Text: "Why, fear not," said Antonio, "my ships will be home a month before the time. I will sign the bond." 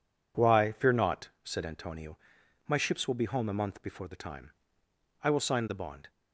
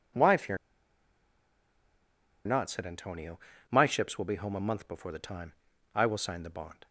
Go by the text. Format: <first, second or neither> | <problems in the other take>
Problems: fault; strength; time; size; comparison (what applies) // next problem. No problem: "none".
first | pauses between "fear" and "not"; strong; at 0.5 s; 1.9 s long